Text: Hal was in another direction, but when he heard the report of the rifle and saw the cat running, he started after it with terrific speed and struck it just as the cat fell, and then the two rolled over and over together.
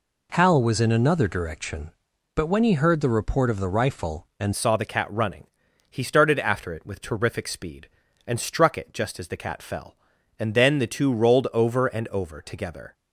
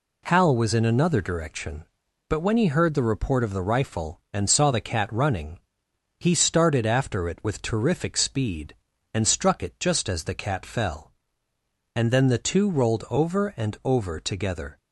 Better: second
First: changes voice at "saw"; from 4.5 s on; 8.4 s long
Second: none

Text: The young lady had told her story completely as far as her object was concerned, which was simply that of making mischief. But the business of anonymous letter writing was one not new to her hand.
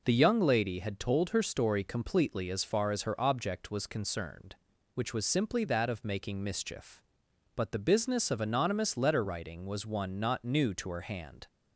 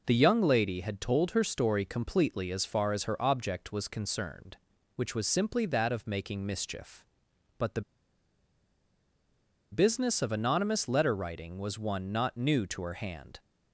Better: first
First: none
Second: pauses between "the" and "business"; strong; at 7.8 s; 1.9 s long

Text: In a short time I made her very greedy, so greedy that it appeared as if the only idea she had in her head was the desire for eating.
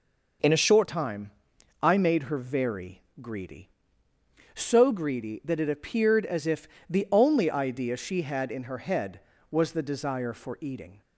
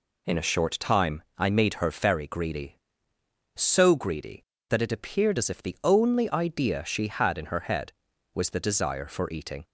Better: second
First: changes voice at "time"; from 0.8 s on; 10.2 s long // pauses between "time" and "I"; noticeable; at 1.3 s; 0.50 s long // pauses between "very" and "greedy"; slight; at 3.0 s; 0.20 s long // pauses between "if" and "the"; slight; at 6.6 s; 0.22 s long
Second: pauses between "time" and "I"; slight; at 1.2 s; 0.16 s long

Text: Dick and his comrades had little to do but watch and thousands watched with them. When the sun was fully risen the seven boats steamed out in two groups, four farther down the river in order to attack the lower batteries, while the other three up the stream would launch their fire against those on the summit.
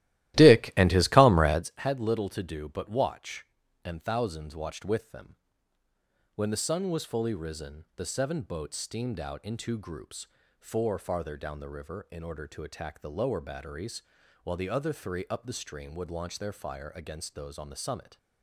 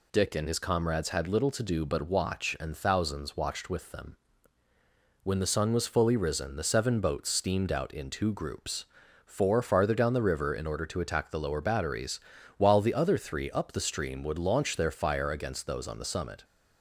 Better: second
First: starts louder than the rest; strong; until 1.7 s; 15.5 dB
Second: none

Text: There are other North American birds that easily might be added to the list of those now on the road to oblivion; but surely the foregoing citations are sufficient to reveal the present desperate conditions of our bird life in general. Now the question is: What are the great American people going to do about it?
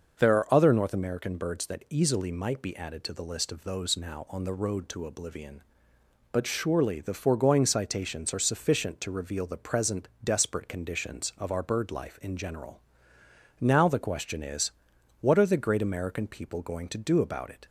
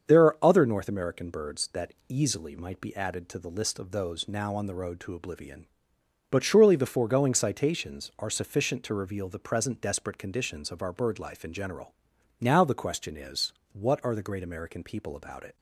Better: first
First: starts louder than the rest; noticeable; until 1.2 s; 6 dB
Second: starts louder than the rest; until 1.1 s; 7 dB // skips "going to do"; at 15.1 s

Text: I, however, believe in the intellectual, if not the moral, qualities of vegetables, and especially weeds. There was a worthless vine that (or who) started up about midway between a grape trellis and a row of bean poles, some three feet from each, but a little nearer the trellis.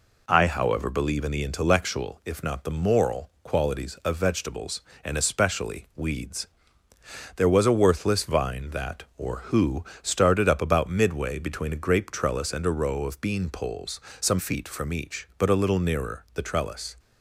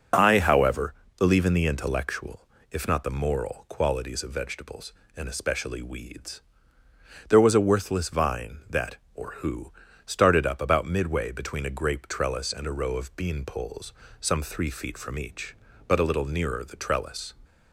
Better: second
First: skips "three"; at 14.3 s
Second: none

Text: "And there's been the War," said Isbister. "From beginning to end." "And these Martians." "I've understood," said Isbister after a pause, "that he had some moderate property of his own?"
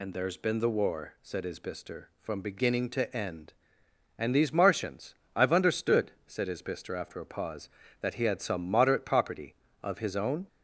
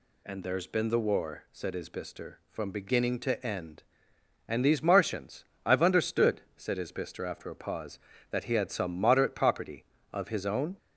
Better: second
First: loses the start of "And"; at 0.0 s; 50 ms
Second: none

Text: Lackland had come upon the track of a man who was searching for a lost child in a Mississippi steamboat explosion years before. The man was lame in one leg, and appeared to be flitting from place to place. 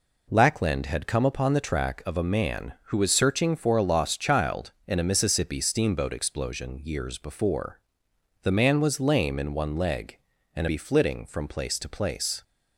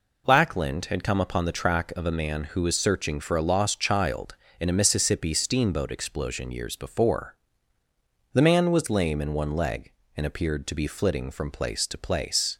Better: second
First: skips "appeared to"; at 10.6 s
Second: none

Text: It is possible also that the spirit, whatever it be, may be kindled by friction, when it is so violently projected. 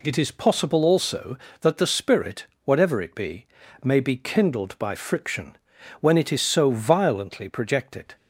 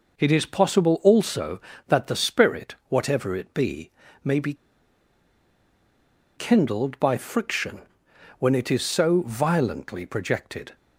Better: first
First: none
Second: pauses between "be" and "kindled"; strong; at 4.5 s; 1.8 s long

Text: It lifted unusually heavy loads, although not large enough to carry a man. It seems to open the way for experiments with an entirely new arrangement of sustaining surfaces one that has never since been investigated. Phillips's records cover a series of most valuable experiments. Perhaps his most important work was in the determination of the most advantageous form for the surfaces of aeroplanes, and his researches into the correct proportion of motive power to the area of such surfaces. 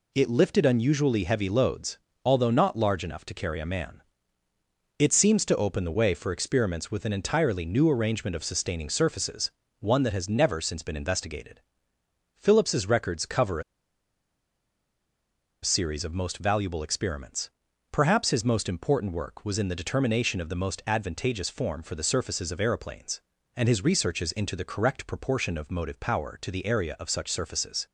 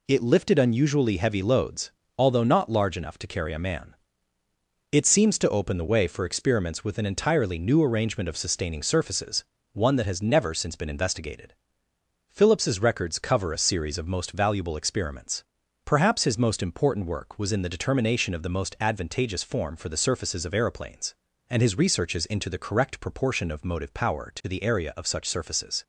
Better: second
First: pauses between "surfaces" and "one"; slight; at 9.5 s; 0.30 s long // pauses between "a" and "series"; strong; at 13.6 s; 2.0 s long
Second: pauses between "surfaces" and "one"; slight; at 9.4 s; 0.30 s long

